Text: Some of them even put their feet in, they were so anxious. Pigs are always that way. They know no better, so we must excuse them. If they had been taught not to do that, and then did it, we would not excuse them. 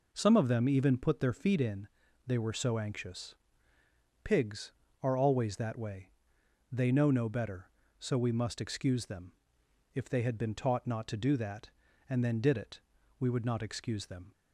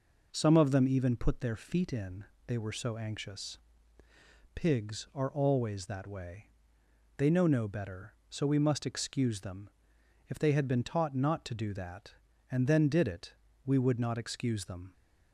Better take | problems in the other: neither | none

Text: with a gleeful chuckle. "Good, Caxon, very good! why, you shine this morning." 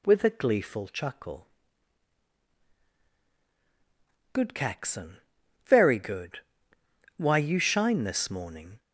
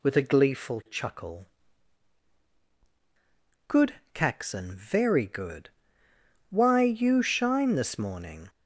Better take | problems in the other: neither | none

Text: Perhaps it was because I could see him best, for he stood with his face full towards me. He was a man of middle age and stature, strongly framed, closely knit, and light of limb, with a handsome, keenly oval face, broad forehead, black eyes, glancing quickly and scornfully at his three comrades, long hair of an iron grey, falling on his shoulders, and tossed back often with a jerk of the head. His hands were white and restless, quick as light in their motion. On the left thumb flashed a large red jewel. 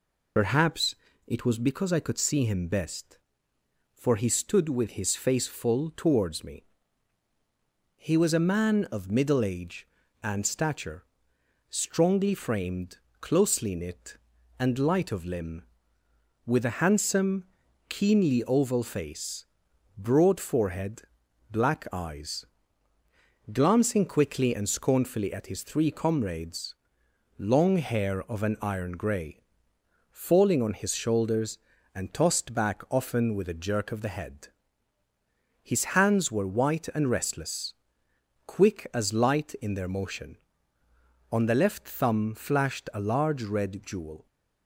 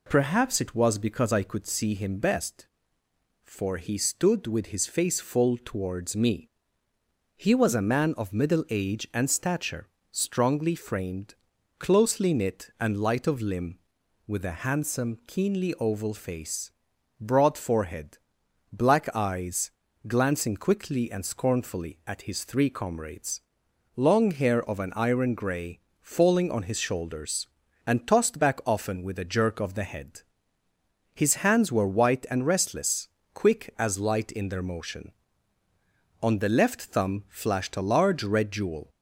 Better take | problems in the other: second | loses the start of "Perhaps"; at 0.3 s; 70 ms // pauses between "Perhaps" and "it"; slight; at 0.9 s; 0.32 s long

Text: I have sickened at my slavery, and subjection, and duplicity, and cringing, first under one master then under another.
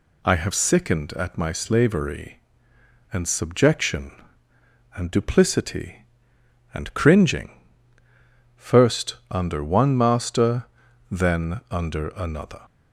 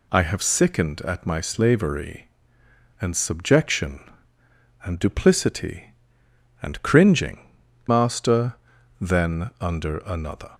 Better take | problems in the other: first | skips "first under one"; at 7.6 s // pauses between "master" and "then"; at 8.5 s; 0.44 s long; also in the first

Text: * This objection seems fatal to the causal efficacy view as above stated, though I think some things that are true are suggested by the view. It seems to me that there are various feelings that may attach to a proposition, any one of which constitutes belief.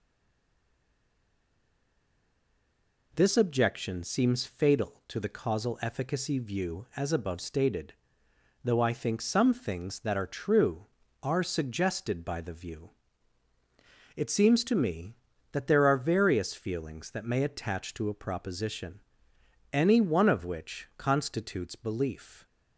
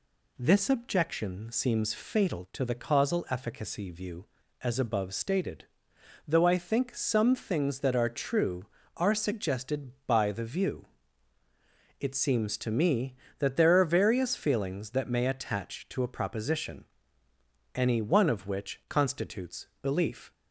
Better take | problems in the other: second | stays silent before the first word; strong; until 3.1 s; 3.1 s long

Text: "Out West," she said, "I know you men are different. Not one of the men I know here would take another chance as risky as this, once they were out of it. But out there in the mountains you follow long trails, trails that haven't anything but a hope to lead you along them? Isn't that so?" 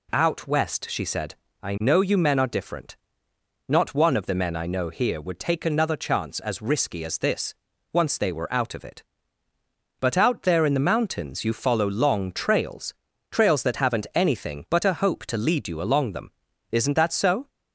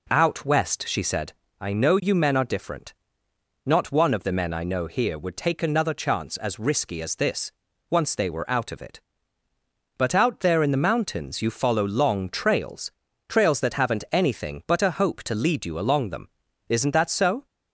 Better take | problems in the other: first | starts louder than the rest; until 1.3 s; 3.5 dB

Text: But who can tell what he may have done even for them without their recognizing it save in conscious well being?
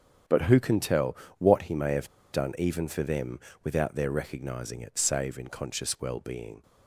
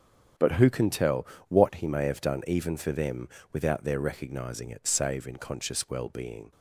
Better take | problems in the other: second | starts louder than the rest; strong; until 1.5 s; 8 dB; strong in the second // pauses between "tell" and "what"; slight; at 1.1 s; 0.22 s long; slight in the second // pauses between "have" and "done"; slight; at 2.0 s; 0.23 s long // pauses between "them" and "without"; slight; at 3.3 s; 0.24 s long; slight in the second

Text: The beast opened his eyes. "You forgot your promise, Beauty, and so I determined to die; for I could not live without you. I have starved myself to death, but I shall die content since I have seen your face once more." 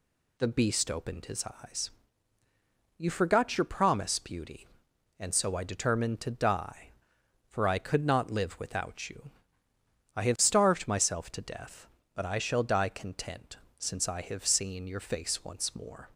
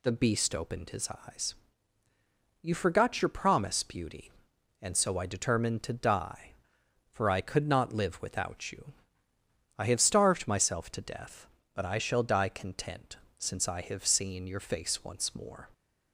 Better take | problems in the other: neither | pauses between "content" and "since"; slight; the same in both

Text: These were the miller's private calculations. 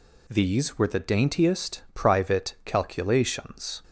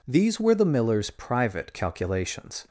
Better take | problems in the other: second | says "daintiest" for "miller's"; at 0.9 s

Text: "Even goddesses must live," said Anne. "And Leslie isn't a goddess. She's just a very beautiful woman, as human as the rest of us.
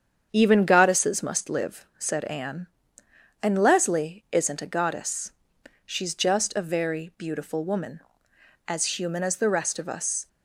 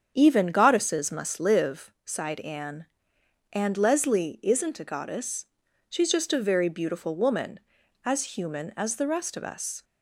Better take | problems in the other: first | starts louder than the rest; strong; until 1.1 s; 7.5 dB; strong in the first // says "sighed" for "said"; at 2.0 s

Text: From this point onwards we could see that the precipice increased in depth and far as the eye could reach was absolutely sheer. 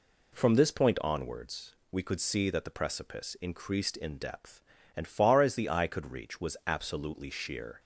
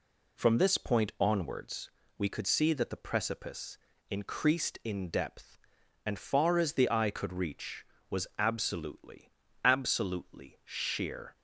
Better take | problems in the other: first | pauses between "onwards" and "we"; slight; at 1.8 s; 0.28 s long; slight in the first // pauses between "precipice" and "increased"; slight; at 3.7 s; 0.32 s long // says "absolutely" twice; at 9.6 s

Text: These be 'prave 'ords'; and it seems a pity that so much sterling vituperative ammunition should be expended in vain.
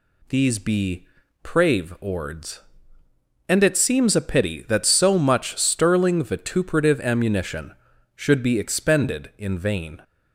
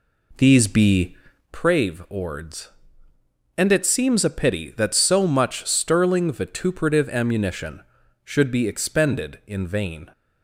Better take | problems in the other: first | starts louder than the rest; slight; until 1.6 s; 2.5 dB // pauses between "be" and "prave"; slight; at 1.1 s; 0.34 s long; slight in the first

